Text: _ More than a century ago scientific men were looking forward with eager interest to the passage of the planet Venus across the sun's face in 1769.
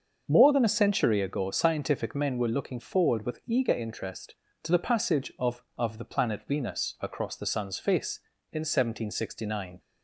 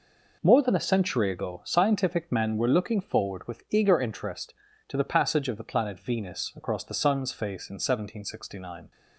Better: second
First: starts louder than the rest; until 1.2 s; 6.5 dB // says "of" twice; at 5.7 s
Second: none

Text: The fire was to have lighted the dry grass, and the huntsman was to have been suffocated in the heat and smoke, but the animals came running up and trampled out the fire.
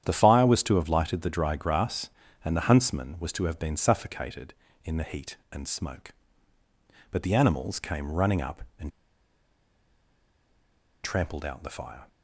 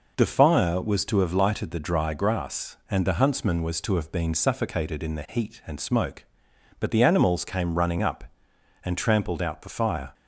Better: second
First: starts louder than the rest; strong; until 1.0 s; 9.5 dB // pauses between "and" and "trampled"; strong; at 8.9 s; 2.1 s long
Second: none

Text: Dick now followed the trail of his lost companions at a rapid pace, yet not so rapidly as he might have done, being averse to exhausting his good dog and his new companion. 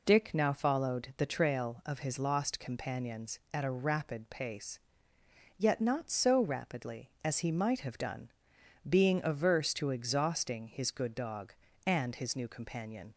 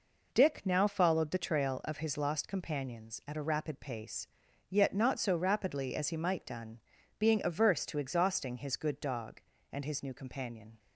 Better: first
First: none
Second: skips "have"; at 6.4 s

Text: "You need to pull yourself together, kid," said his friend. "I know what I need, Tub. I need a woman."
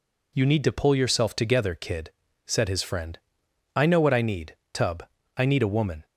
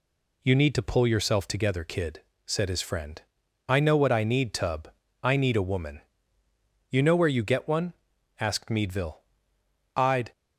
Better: first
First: none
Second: goes on to say "You know where you get one asked Meadville I'd"; strong; from 6.8 s on; 3.4 s long

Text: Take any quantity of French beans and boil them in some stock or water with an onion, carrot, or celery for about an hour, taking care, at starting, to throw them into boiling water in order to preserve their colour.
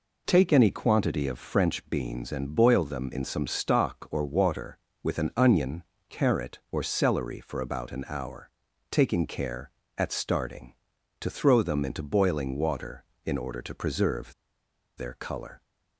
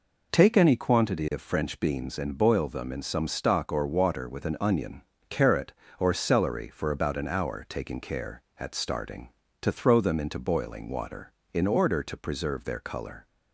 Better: second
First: pauses between "preserve" and "their"; noticeable; at 14.3 s; 0.64 s long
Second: none

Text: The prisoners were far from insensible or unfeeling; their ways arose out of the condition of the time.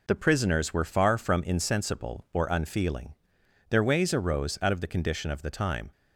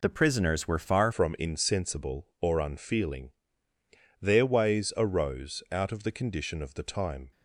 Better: first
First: none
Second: changes voice at "from"; from 1.1 s on; 6.2 s long

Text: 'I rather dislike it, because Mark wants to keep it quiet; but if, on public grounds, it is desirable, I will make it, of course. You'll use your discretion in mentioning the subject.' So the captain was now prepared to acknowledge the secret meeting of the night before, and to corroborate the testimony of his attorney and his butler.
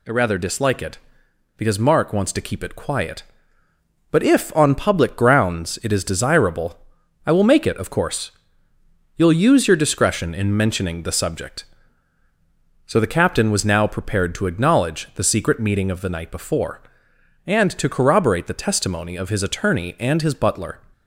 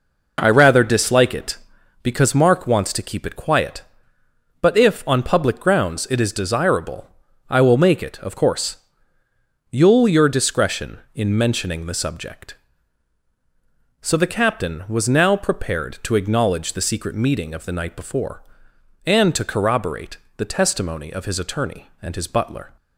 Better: first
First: none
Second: skips "use"; at 10.0 s // pauses between "corroborate" and "the"; slight; at 20.1 s; 0.22 s long

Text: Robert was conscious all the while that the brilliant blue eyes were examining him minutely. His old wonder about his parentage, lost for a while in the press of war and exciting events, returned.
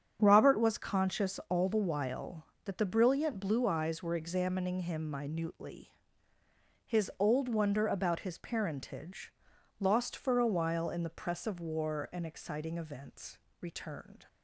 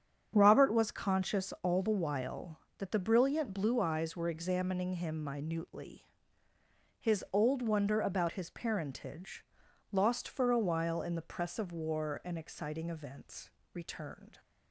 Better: neither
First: starts louder than the rest; strong; until 1.2 s; 8 dB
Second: starts louder than the rest; strong; until 1.3 s; 8 dB

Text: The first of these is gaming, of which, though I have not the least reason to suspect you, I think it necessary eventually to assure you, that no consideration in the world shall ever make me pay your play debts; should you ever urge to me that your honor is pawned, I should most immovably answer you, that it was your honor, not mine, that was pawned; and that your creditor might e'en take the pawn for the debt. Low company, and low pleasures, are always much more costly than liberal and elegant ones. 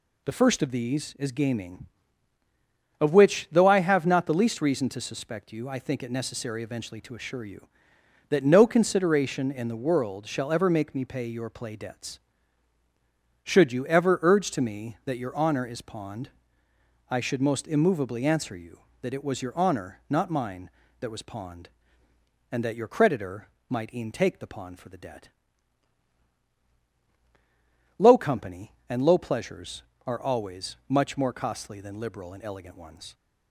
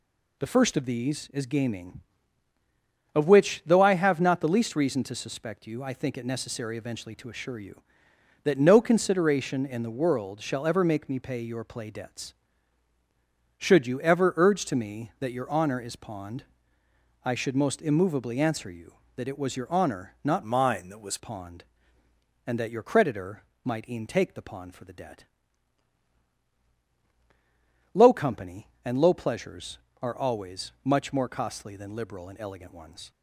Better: first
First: pauses between "creditor" and "might"; slight; at 23.4 s; 0.20 s long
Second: changes voice from "mine" to "was"; from 20.4 to 21.1 s; 0.7 s long // pauses between "creditor" and "might"; slight; at 23.4 s; 0.20 s long

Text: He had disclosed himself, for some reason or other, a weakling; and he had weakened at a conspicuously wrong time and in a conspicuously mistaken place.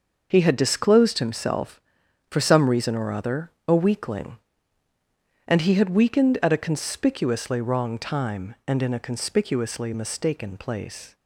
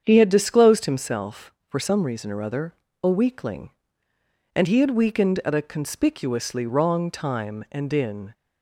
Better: first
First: starts louder than the rest; noticeable; until 1.3 s; 6 dB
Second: starts louder than the rest; strong; until 1.0 s; 7.5 dB // stops before "a conspicuously mistaken place"; at 8.3 s

